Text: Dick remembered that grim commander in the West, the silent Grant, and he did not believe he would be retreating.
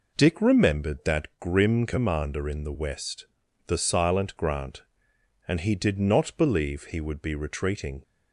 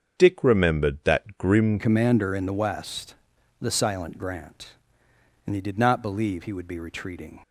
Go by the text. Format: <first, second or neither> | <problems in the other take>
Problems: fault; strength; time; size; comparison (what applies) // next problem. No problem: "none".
first | starts louder than the rest; strong; until 1.2 s; 7 dB // changes voice at "commander"; from 1.7 s on; 5.6 s long